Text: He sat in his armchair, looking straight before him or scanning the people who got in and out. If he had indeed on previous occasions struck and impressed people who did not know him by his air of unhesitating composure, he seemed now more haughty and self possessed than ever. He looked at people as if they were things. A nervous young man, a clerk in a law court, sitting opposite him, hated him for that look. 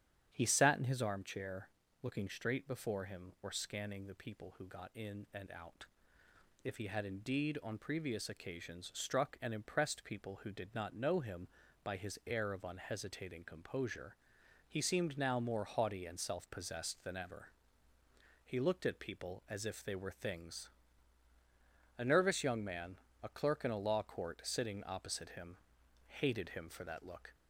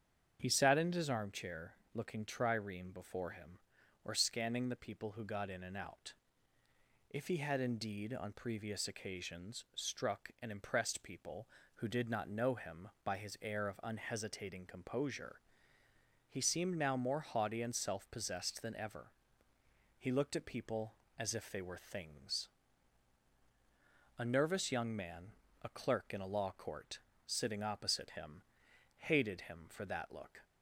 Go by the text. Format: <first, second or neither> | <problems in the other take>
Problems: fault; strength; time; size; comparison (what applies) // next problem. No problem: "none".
first | starts louder than the rest; strong; until 1.4 s; 8 dB; strong in the first // says "trireme" for "straight"; at 2.2 s